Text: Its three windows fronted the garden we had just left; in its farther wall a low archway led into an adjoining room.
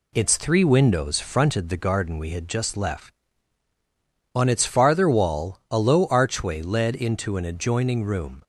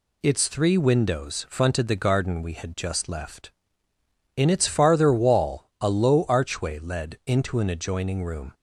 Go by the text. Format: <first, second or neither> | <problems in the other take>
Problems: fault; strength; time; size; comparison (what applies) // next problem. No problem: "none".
second | says "on" for "in"; at 4.3 s